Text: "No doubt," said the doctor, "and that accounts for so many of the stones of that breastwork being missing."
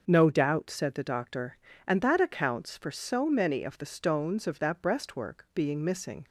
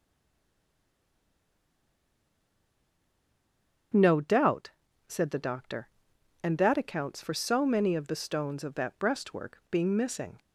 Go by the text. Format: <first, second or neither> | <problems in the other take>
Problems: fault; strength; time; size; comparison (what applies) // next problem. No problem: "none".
first | stays silent before the first word; strong; until 3.9 s; 3.9 s long // starts louder than the rest; strong; until 5.3 s; 7.5 dB; noticeable in the first